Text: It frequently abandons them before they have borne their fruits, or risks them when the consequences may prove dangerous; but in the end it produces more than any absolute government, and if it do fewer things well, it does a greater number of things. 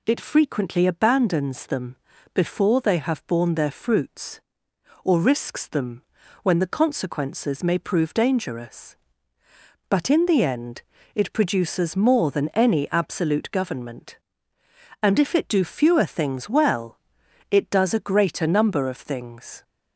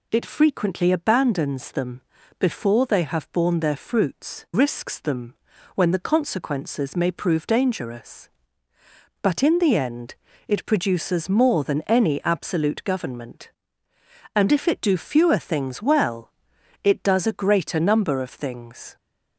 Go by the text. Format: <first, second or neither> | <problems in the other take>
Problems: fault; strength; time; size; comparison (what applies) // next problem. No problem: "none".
first | pauses between "them" and "before"; at 2.0 s; 0.38 s long; also in the first // skips "or"; at 4.4 s // pauses between "them" and "when"; at 5.3 s; 0.40 s long; also in the first // pauses between "end" and "it"; slight; at 10.1 s; 0.32 s long; slight in the first